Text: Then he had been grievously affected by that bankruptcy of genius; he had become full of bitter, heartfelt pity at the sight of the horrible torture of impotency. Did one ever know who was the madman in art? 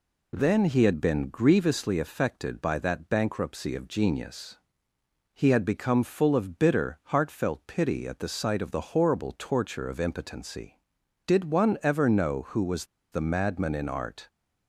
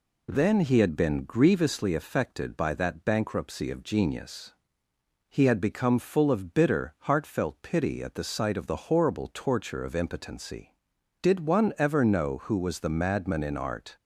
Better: second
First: pauses between "was" and "the"; slight; at 12.8 s; 0.25 s long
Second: none

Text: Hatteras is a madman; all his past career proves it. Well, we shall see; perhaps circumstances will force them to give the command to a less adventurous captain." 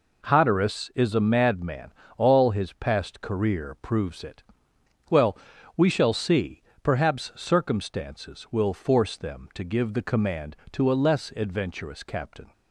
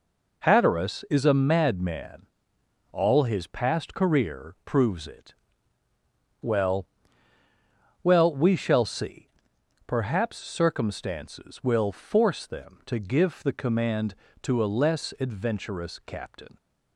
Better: first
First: none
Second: says "Well" twice; at 8.0 s

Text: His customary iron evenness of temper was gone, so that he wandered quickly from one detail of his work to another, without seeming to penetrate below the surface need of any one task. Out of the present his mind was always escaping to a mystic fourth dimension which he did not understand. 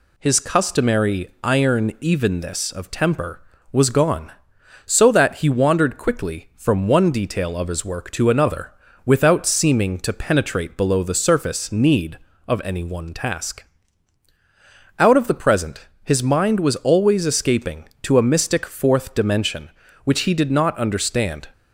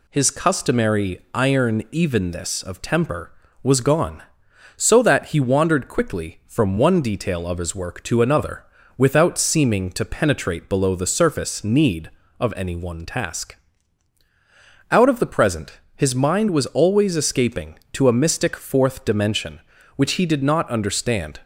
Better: neither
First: pauses between "present" and "his"; slight; at 15.8 s; 0.18 s long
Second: pauses between "present" and "his"; slight; at 15.7 s; 0.18 s long

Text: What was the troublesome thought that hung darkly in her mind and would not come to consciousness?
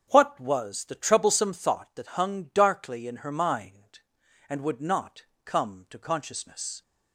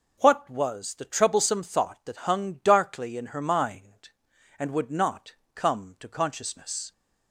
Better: second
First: starts louder than the rest; strong; until 1.8 s; 7 dB // pauses between "not" and "come"; slight; at 5.2 s; 0.18 s long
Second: pauses between "not" and "come"; slight; at 5.3 s; 0.18 s long

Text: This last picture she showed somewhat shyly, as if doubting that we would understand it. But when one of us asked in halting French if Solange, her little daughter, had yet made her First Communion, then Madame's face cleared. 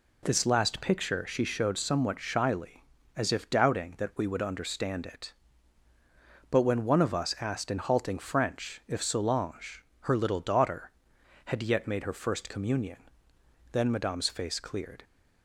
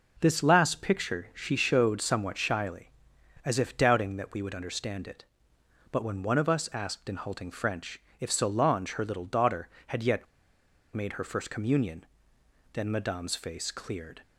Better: first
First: none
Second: pauses between "French" and "if"; slight; at 8.0 s; 0.16 s long // pauses between "yet" and "made"; noticeable; at 10.2 s; 0.68 s long

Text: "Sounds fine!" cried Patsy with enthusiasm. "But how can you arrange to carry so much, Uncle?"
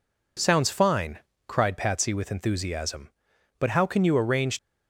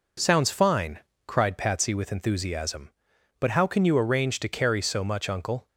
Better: second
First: stops before "to carry so much Uncle"; at 4.5 s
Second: none

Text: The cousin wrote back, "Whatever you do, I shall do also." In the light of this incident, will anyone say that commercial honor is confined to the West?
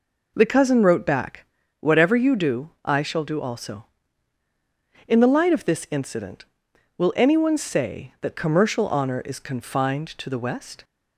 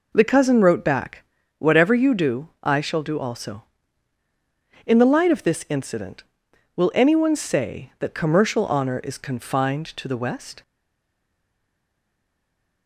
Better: first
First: none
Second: stays silent after the last word; from 10.6 s on; 2.2 s long

